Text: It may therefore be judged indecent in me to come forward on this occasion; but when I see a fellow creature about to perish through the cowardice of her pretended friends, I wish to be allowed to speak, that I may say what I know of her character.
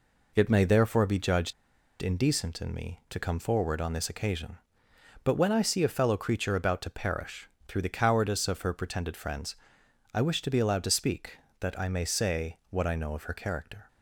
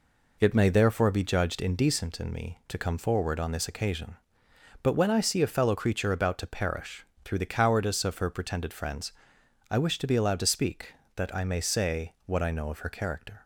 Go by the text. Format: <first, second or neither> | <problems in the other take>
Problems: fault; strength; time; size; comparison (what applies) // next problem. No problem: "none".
second | pauses between "judged" and "indecent"; noticeable; at 1.5 s; 0.48 s long // pauses between "perish" and "through"; slight; at 7.4 s; 0.18 s long; slight in the second